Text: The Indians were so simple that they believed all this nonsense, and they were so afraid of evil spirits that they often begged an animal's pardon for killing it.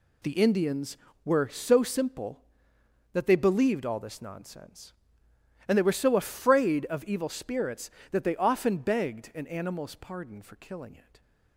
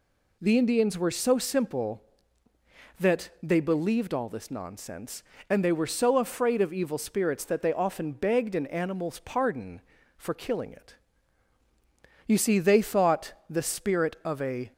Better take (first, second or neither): first